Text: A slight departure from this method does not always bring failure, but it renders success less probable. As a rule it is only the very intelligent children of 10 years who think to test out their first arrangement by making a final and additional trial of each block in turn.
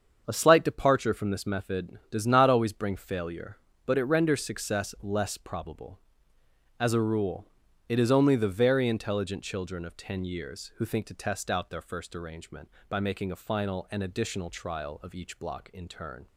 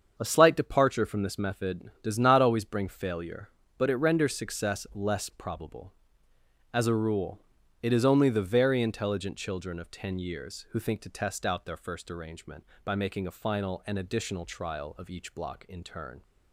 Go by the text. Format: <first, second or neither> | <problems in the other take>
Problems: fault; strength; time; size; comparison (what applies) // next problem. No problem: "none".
neither | starts louder than the rest; strong; the same in both // pauses between "rule" and "it"; the same in both